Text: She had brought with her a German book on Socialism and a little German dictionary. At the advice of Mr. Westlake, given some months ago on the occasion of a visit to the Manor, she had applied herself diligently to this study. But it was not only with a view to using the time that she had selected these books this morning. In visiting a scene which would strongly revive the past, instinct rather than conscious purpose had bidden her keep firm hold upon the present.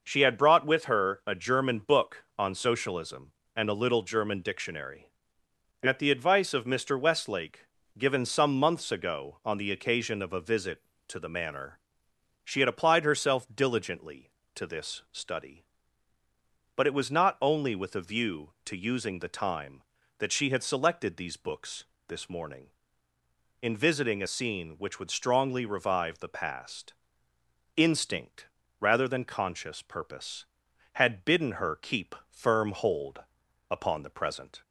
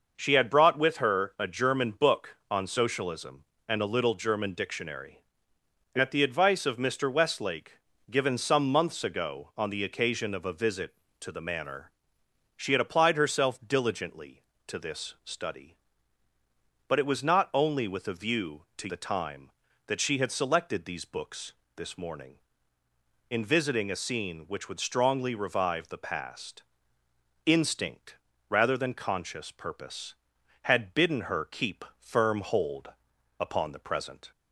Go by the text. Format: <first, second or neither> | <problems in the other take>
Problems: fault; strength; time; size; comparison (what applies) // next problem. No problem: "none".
first | skips "using"; at 18.8 s // pauses between "books" and "this"; slight; at 21.5 s; 0.22 s long; slight in the first // pauses between "instinct" and "rather"; slight; at 28.1 s; 0.34 s long; slight in the first // pauses between "hold" and "upon"; noticeable; at 32.8 s; 0.50 s long; noticeable in the first